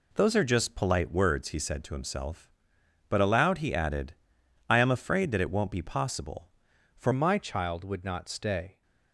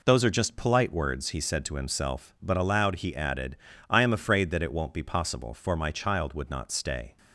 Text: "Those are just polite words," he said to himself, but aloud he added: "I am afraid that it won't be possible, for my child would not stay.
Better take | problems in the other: second | changes voice at "my"; from 7.1 s on; 1.7 s long

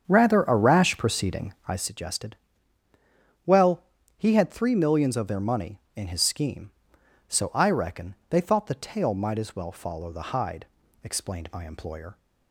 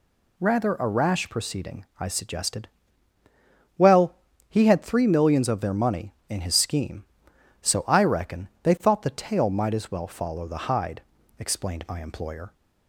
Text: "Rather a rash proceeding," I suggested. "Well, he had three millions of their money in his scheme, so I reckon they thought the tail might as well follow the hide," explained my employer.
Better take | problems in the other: second | starts louder than the rest; strong; until 1.9 s; 7.5 dB

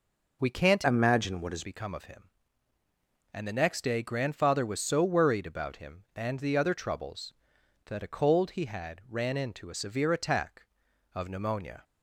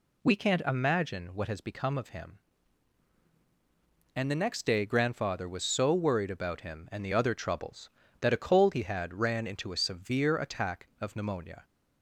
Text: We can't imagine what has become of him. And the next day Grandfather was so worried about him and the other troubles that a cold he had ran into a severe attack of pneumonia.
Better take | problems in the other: second | changes voice from "imagine" to "has"; from 0.8 to 1.6 s; 0.8 s long

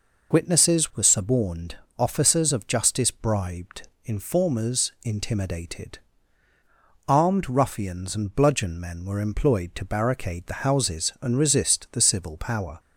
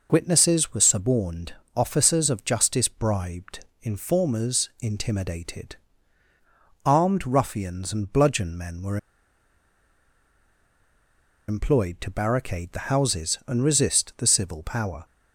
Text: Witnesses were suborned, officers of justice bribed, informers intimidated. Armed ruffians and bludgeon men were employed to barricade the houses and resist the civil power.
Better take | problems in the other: first | pauses between "were" and "employed"; strong; at 8.9 s; 2.5 s long

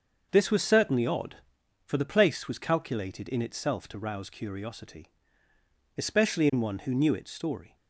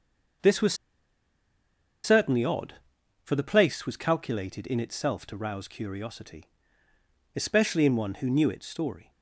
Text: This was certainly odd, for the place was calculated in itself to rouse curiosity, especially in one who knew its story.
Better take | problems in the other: first | starts louder than the rest; until 2.7 s; 6.5 dB; also in the first // pauses between "was" and "certainly"; strong; at 0.7 s; 1.3 s long

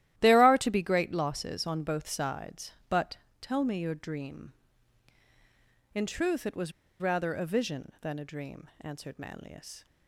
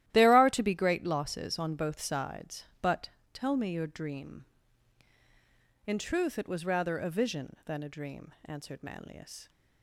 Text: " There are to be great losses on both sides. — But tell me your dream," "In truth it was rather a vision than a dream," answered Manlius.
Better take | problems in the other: second | starts louder than the rest; strong; until 1.1 s; 13.5 dB; strong in the second // pauses between "But" and "tell"; slight; at 3.1 s; 0.22 s long; slight in the second // pauses between "was" and "rather"; slight; at 6.7 s; 0.29 s long

